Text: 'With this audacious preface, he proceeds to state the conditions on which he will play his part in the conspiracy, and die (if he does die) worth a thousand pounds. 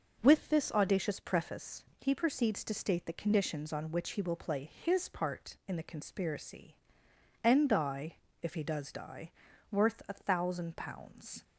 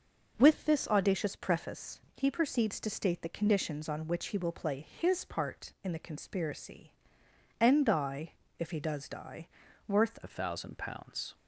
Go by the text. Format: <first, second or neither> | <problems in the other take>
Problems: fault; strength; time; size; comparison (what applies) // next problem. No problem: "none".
first | changes voice at "a"; from 10.2 s on; 1.1 s long